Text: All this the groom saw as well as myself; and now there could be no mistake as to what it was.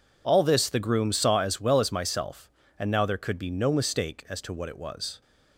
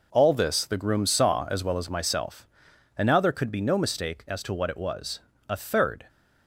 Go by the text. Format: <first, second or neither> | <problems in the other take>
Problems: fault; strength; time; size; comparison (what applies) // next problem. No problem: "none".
first | goes on to say "A third"; from 5.4 s on; 0.60 s long